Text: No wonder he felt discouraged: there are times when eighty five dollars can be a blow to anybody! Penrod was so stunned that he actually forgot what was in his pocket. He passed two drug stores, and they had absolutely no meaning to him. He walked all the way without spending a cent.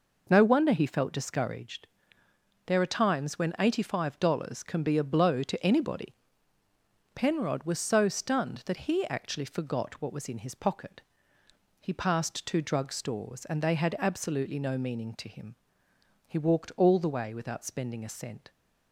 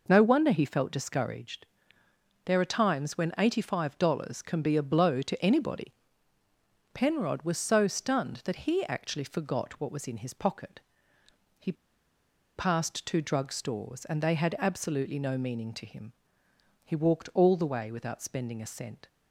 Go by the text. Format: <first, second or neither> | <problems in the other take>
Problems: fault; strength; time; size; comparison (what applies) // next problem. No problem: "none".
first | pauses between "He" and "passed"; noticeable; at 11.7 s; 0.83 s long